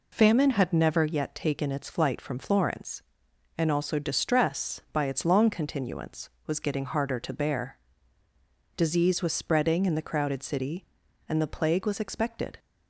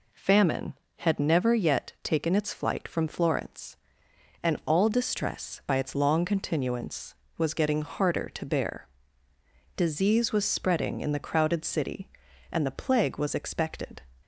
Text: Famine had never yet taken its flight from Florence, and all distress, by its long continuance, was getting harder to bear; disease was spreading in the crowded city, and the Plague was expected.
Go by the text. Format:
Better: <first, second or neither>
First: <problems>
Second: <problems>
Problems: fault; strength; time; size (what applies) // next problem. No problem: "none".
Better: second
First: says "also" for "all"; at 3.7 s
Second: none